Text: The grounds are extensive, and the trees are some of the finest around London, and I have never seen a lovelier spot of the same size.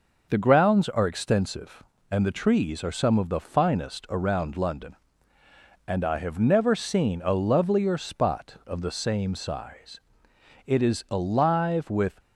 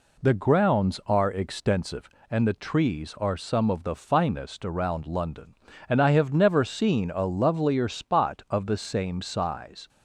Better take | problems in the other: second | goes on to say "It is alive with"; from 10.6 s on; 1.5 s long

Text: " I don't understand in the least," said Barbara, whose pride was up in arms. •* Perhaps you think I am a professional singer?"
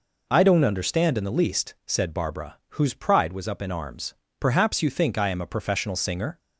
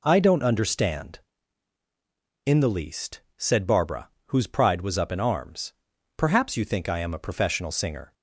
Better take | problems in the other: neither | none

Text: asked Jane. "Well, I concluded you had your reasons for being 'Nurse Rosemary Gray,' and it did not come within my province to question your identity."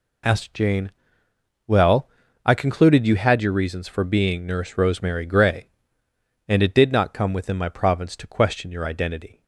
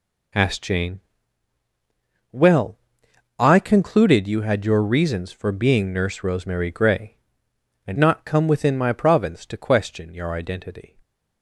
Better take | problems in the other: first | skips "it did"; at 7.9 s

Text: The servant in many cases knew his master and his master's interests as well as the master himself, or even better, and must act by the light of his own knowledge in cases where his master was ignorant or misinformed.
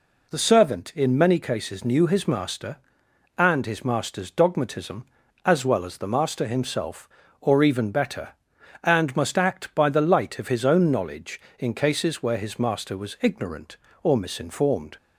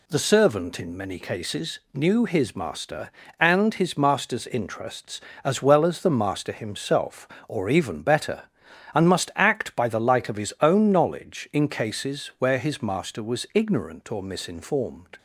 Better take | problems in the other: second | says "dogmatism" for "interests"; at 4.2 s

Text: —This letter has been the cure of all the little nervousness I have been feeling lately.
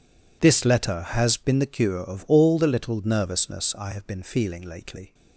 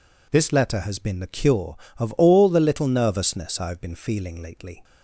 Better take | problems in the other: neither | none

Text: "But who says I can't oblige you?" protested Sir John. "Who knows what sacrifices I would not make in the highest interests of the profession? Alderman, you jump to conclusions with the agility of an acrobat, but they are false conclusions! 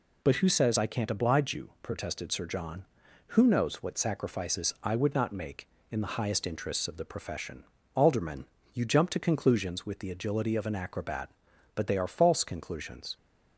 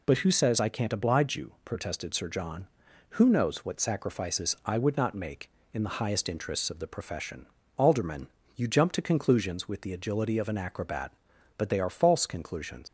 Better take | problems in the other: first | leaves "conclusions" unfinished; at 12.8 s; 105 ms

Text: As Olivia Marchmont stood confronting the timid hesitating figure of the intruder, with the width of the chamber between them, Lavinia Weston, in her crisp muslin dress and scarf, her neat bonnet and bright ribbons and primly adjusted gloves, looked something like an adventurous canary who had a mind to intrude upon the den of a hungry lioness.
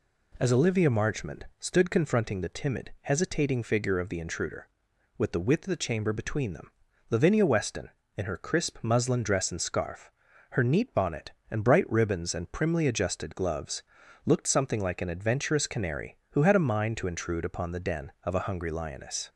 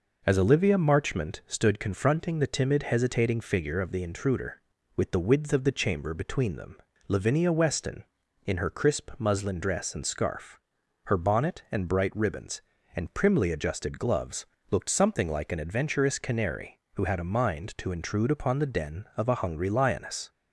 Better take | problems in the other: first | skips "neat"; at 11.1 s

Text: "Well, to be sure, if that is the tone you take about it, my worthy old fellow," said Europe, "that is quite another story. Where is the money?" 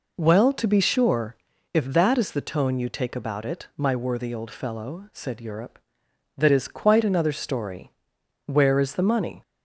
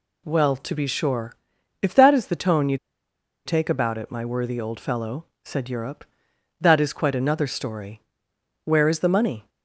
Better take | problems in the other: first | pauses between "you" and "take"; noticeable; at 2.7 s; 0.70 s long

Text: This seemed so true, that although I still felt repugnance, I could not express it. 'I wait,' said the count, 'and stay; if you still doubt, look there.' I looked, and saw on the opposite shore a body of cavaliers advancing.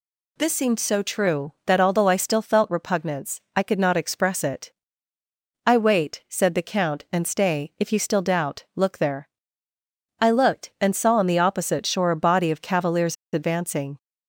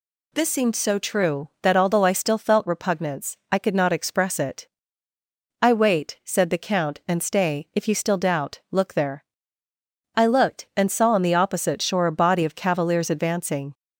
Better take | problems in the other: second | pauses between "cavaliers" and "advancing"; slight; at 13.1 s; 0.17 s long

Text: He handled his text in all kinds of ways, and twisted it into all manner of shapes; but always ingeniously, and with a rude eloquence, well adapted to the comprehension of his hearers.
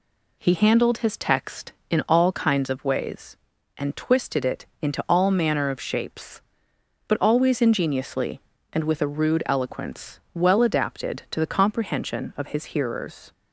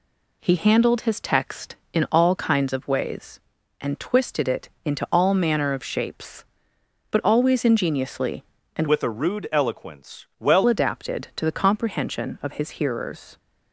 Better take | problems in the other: first | pauses between "it" and "into"; slight; at 4.6 s; 0.16 s long; slight in the first // changes voice from "with" to "well"; from 8.8 to 10.6 s; 1.8 s long

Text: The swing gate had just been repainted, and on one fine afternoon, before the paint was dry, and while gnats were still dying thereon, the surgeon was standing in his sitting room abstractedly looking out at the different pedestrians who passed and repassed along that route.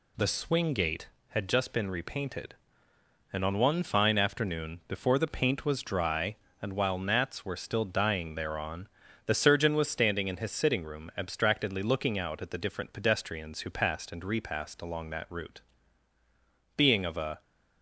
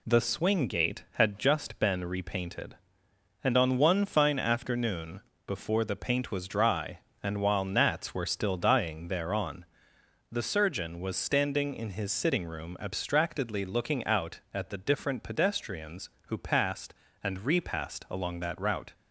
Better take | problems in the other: second | goes on to say "Being of a"; noticeable; from 16.7 s on; 0.64 s long

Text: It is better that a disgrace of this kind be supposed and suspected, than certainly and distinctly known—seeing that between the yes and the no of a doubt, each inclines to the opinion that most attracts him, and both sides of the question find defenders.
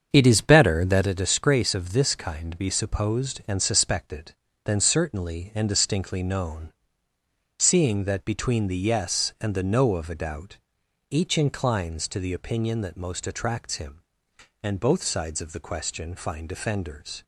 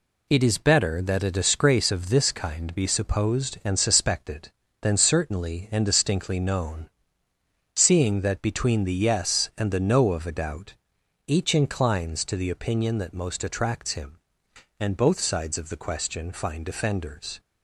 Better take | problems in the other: second | starts louder than the rest; strong; until 1.1 s; 7 dB

